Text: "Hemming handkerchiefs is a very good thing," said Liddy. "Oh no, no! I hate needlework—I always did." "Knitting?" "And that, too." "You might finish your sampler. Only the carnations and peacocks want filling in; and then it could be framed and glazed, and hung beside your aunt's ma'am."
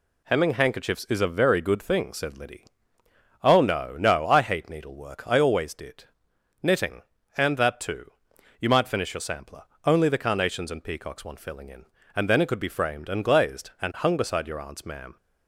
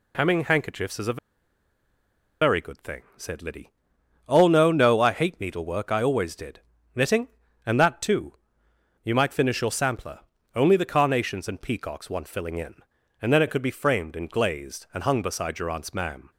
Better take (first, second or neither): first